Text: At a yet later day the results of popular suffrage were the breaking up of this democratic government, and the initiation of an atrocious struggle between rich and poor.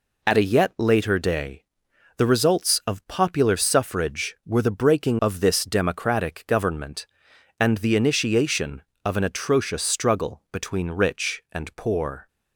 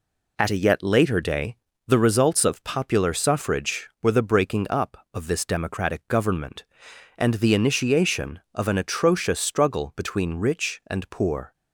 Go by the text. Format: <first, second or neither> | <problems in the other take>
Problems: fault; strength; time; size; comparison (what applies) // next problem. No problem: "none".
second | pauses between "day" and "the"; noticeable; at 1.6 s; 0.54 s long; slight in the second // skips "up"; at 5.2 s